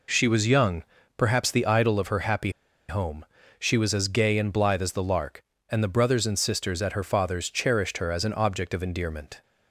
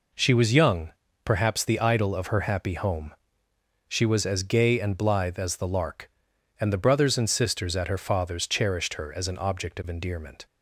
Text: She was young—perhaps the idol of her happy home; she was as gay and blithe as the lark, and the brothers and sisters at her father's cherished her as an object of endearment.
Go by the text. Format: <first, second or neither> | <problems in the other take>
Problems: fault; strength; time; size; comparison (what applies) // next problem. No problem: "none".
second | pauses between "happy" and "home"; at 2.4 s; 0.39 s long